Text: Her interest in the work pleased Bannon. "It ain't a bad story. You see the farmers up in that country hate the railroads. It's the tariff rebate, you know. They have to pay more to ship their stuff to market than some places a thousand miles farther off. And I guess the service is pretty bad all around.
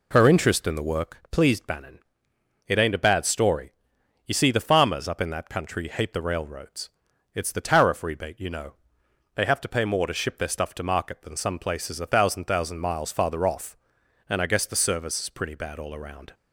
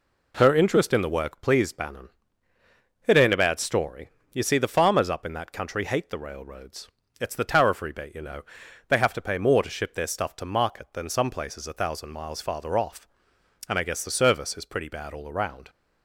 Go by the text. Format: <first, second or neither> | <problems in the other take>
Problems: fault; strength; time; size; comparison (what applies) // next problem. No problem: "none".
second | says "thousand" twice; at 12.4 s